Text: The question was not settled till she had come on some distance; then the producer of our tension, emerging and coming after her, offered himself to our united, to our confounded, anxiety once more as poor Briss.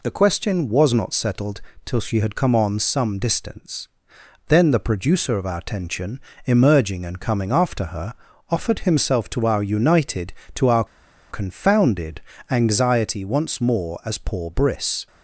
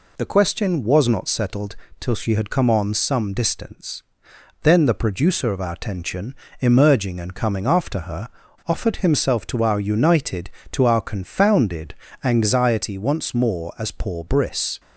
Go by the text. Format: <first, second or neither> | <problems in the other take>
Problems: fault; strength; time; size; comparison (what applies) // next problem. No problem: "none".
second | pauses between "settled" and "till"; slight; at 1.6 s; 0.24 s long; slight in the second // pauses between "our" and "confounded"; noticeable; at 10.8 s; 0.46 s long